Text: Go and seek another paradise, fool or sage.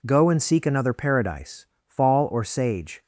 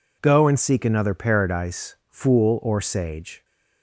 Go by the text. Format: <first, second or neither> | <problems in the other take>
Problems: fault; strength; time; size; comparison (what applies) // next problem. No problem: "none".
second | says "fall" for "fool"; at 1.8 s